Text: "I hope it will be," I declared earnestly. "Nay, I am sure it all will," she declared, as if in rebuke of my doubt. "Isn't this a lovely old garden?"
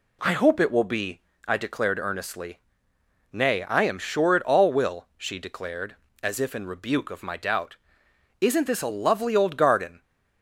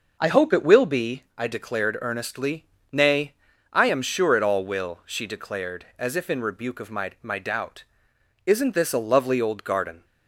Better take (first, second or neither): first